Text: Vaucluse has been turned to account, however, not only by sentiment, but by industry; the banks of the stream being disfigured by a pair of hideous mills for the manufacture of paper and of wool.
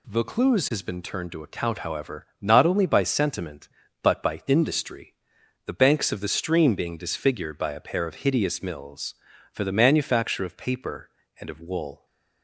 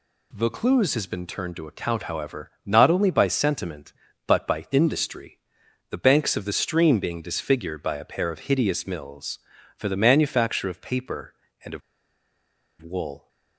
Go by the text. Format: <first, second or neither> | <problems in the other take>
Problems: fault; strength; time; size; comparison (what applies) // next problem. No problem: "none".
first | pauses between "of" and "wool"; at 11.8 s; 1.0 s long